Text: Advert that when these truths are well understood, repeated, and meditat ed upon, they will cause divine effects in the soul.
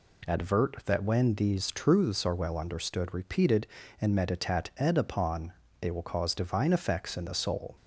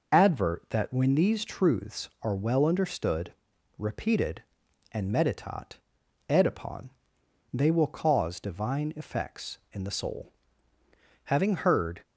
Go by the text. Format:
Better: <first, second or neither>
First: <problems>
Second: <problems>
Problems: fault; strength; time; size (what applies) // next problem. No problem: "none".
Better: first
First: none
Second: pauses between "meditat" and "ed"; noticeable; at 5.7 s; 0.52 s long // goes on to say "Having heard"; noticeable; from 11.2 s on; 0.76 s long